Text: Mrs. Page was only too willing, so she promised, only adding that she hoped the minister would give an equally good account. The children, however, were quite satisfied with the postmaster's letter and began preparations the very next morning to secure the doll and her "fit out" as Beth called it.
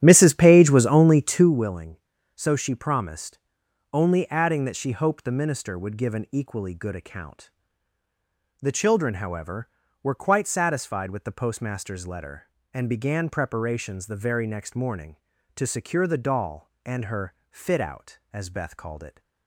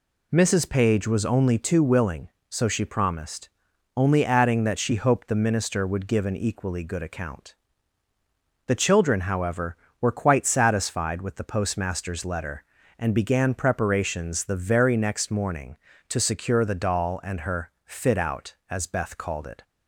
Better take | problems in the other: second | starts louder than the rest; strong; until 1.5 s; 10.5 dB // pauses between "her" and "fit"; slight; at 17.3 s; 0.16 s long

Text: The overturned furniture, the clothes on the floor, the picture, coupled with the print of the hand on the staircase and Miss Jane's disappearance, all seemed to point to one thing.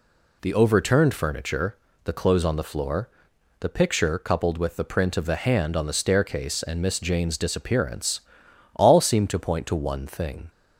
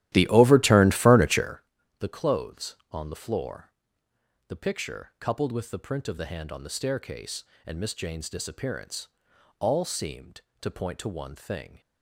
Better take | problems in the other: first | starts louder than the rest; strong; until 1.7 s; 13.5 dB

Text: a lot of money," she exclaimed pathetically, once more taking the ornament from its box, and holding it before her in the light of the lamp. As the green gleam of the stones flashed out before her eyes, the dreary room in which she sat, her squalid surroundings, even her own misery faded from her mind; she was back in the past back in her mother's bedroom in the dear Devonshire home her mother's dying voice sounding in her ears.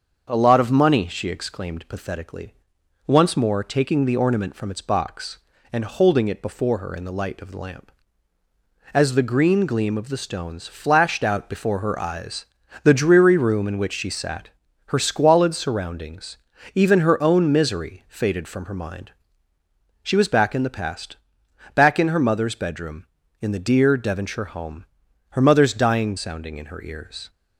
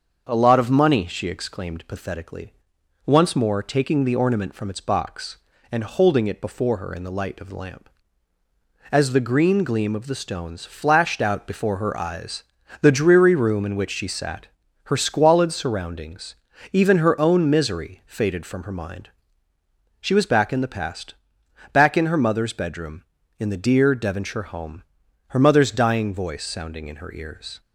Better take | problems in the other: second | starts louder than the rest; until 1.3 s; 7 dB; also in the second // pauses between "past" and "back"; noticeable; at 21.1 s; 0.58 s long; noticeable in the second // pauses between "home" and "her"; noticeable; at 24.8 s; 0.46 s long; noticeable in the second // skips "voice"; at 26.1 s

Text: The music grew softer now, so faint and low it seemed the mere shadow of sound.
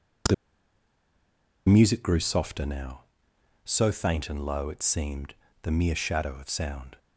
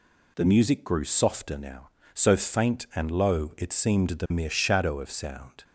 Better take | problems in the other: second | pauses between "The" and "music"; strong; at 0.3 s; 1.3 s long // pauses between "seemed" and "the"; slight; at 5.3 s; 0.28 s long

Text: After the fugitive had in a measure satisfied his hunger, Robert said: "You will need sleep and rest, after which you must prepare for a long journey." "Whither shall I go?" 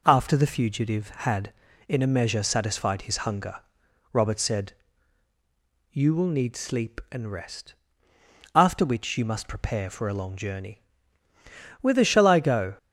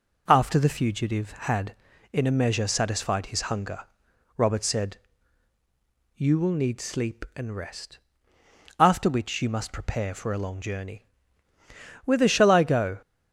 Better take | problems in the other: neither | none

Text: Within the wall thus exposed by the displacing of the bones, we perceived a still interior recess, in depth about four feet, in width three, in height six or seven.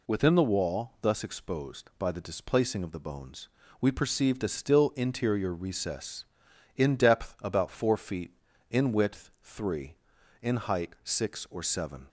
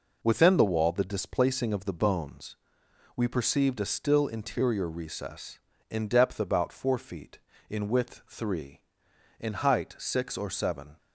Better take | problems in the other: first | skips "thus exposed by"; at 0.9 s

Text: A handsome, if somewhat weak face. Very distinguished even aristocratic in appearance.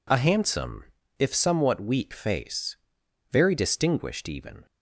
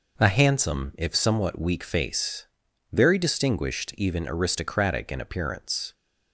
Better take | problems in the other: second | stops before "aristocratic in appearance"; at 4.6 s

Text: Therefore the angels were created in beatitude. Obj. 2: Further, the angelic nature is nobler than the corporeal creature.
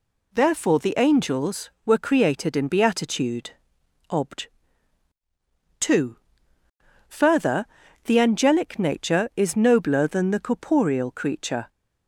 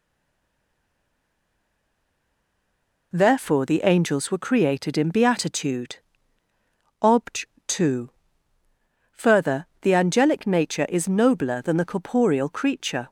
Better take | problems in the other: first | stays silent before the first word; strong; until 3.1 s; 3.1 s long

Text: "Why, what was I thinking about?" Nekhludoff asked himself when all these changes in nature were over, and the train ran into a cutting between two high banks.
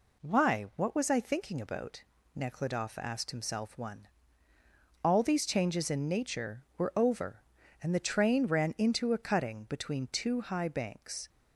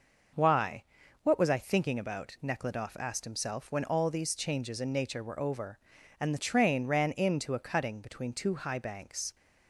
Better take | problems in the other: second | says "one" for "when"; at 3.7 s

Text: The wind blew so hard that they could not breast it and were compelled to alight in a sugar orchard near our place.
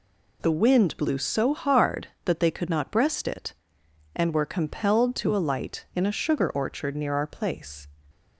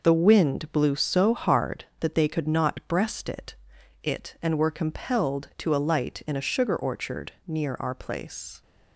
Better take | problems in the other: first | says "it" twice; at 4.0 s // pauses between "orchard" and "near"; slight; at 7.3 s; 0.16 s long

